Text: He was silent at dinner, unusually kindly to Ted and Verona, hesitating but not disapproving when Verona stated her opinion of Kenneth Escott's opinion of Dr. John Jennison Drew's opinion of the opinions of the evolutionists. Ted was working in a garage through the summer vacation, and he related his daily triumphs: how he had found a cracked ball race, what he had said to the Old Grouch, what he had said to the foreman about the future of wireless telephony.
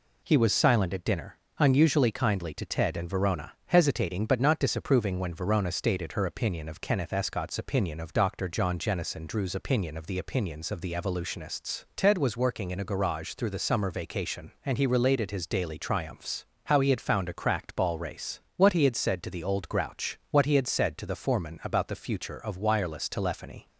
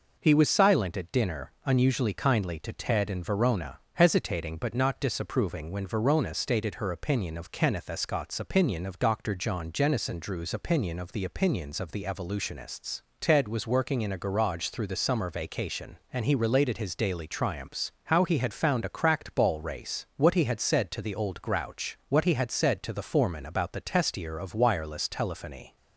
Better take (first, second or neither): first